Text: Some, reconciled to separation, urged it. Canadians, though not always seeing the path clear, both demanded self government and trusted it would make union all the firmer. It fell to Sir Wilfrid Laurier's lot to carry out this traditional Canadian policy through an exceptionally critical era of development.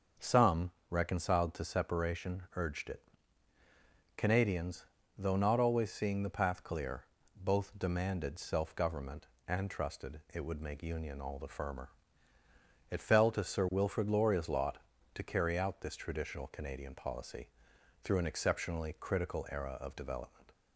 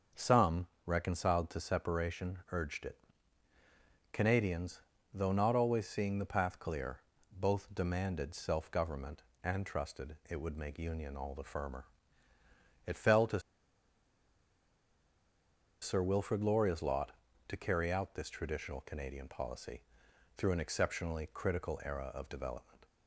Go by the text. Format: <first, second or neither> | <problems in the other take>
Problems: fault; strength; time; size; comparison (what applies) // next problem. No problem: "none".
first | starts louder than the rest; until 1.3 s; 6.5 dB; also in the first // pauses between "to" and "Sir"; strong; at 13.3 s; 2.4 s long // pauses between "policy" and "through"; noticeable; at 19.8 s; 0.56 s long; noticeable in the first